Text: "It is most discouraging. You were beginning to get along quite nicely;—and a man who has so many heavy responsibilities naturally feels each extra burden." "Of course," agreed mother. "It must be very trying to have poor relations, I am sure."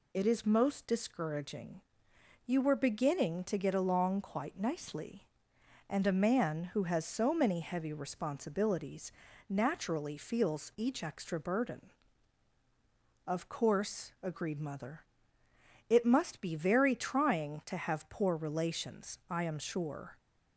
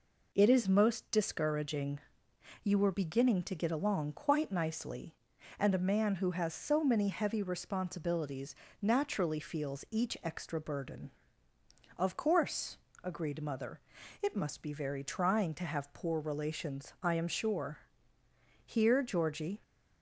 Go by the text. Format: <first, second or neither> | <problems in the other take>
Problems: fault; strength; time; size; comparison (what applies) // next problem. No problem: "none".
first | pauses between "responsibilities" and "naturally"; slight; at 8.5 s; 0.28 s long; also in the first // goes on to say "Here Georgie"; noticeable; from 18.6 s on; 0.96 s long